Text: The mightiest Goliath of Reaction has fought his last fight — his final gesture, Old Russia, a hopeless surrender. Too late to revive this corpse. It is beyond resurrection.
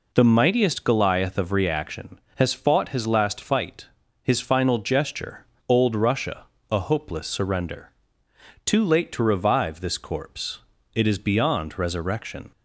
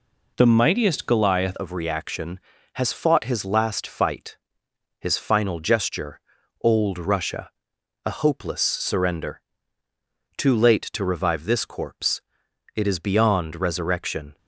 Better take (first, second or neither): first